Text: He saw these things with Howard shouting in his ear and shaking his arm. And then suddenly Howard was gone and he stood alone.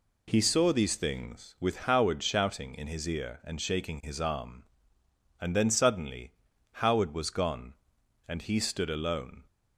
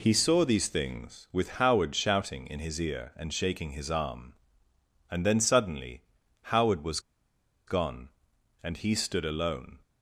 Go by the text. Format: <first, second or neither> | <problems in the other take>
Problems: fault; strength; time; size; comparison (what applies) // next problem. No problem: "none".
first | pauses between "suddenly" and "Howard"; at 6.0 s; 0.44 s long; also in the first // pauses between "was" and "gone"; noticeable; at 6.9 s; 0.68 s long